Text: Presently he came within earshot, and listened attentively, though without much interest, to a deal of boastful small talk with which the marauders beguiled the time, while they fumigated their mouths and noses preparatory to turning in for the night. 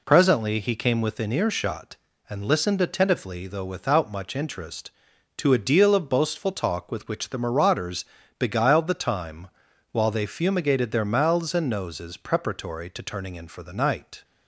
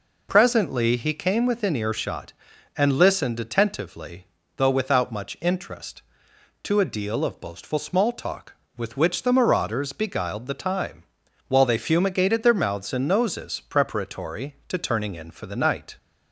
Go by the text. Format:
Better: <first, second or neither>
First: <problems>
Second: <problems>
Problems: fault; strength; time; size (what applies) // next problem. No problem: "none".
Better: second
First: skips "small"; at 6.5 s // pauses between "marauders" and "beguiled"; slight; at 8.0 s; 0.34 s long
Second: none